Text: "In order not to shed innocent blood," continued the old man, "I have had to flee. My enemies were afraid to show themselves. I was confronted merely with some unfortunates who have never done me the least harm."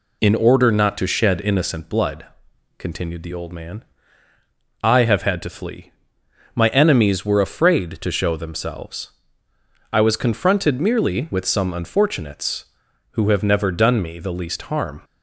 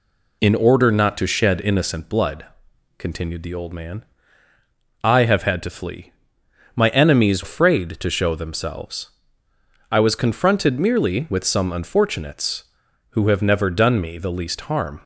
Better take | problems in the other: first | skips "were"; at 7.4 s

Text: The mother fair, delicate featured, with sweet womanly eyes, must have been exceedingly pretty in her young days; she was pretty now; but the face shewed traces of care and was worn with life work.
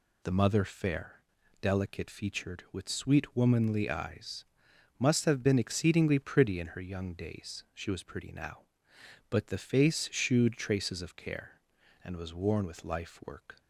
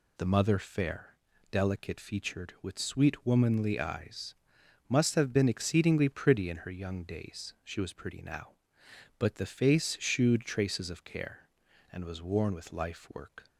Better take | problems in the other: neither | none

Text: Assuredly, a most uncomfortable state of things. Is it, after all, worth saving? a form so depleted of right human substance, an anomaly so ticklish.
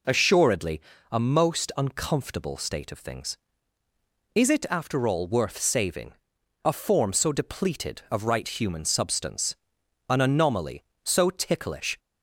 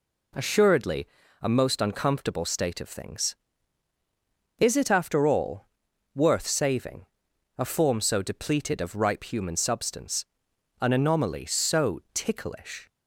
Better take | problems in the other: first | says "ripe" for "right"; at 8.9 s

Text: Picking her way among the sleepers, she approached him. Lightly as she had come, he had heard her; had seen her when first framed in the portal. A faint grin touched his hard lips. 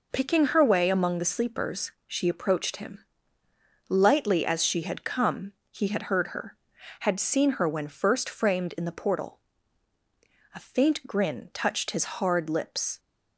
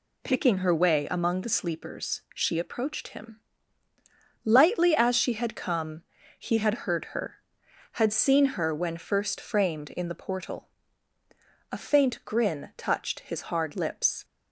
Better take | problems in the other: neither | none

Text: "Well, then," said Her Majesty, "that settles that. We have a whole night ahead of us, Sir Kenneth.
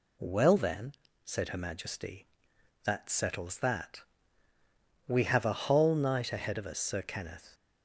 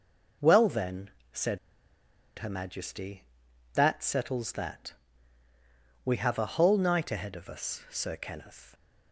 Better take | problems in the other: first | pauses between "said" and "Her"; noticeable; at 1.5 s; 0.80 s long

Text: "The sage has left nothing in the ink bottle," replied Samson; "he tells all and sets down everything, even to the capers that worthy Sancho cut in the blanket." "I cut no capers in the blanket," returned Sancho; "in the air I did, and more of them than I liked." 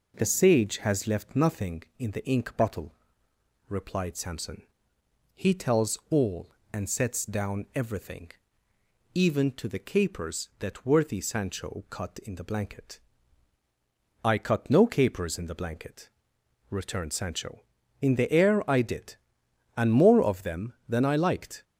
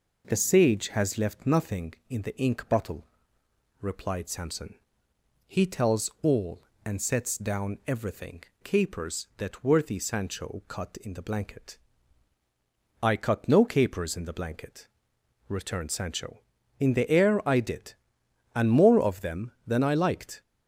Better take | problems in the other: first | skips "even to the"; at 8.5 s

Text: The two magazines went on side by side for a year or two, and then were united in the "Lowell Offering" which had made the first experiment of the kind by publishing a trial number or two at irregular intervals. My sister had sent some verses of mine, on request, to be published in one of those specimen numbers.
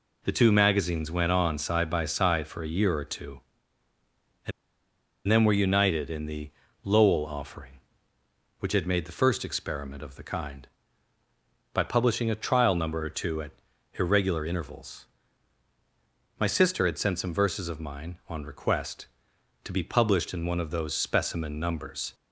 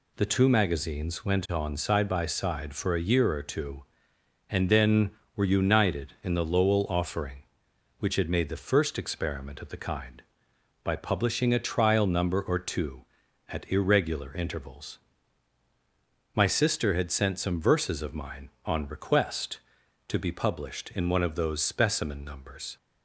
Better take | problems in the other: second | pauses between "and" and "then"; noticeable; at 4.5 s; 0.76 s long // pauses between "the" and "Lowell"; slight; at 6.5 s; 0.34 s long // pauses between "at" and "irregular"; noticeable; at 13.5 s; 0.48 s long

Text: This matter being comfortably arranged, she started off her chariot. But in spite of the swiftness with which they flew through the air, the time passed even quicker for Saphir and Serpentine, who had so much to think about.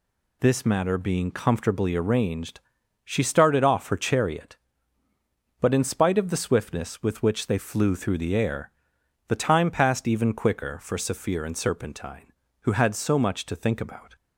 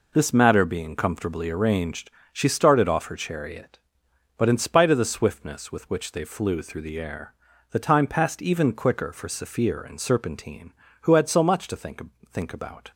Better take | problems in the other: first | says "think" twice; at 12.3 s

